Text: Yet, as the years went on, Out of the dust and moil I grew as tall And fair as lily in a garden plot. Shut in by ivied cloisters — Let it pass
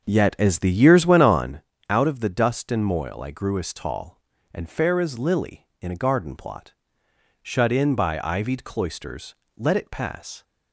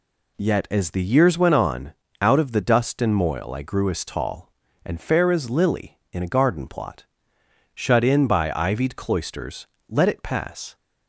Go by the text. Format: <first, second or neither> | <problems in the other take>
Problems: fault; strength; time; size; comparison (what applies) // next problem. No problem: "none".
second | starts louder than the rest; until 1.7 s; 6.5 dB